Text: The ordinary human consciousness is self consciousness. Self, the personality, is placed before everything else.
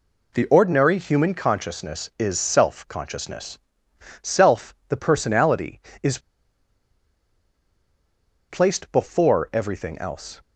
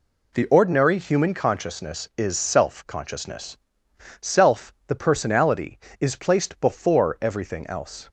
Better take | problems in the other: second | pauses between "is" and "placed"; strong; at 6.1 s; 2.3 s long

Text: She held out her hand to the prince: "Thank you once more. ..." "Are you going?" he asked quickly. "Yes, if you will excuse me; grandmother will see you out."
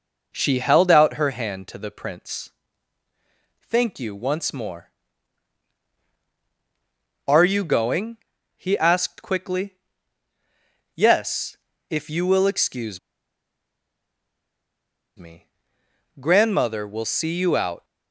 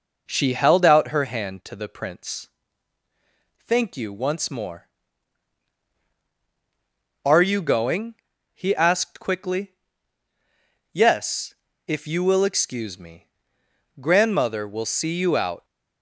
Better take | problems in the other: second | pauses between "excuse" and "me"; strong; at 12.9 s; 2.1 s long

